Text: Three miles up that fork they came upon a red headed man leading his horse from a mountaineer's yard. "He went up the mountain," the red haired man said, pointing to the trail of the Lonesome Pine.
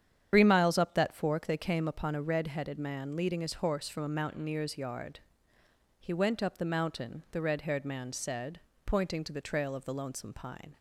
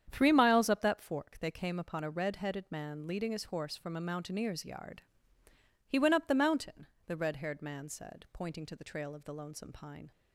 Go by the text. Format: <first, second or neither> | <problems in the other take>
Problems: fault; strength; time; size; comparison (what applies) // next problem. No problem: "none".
second | loses the start of "Three"; at 0.3 s; 90 ms // starts louder than the rest; strong; until 1.3 s; 9 dB; strong in the second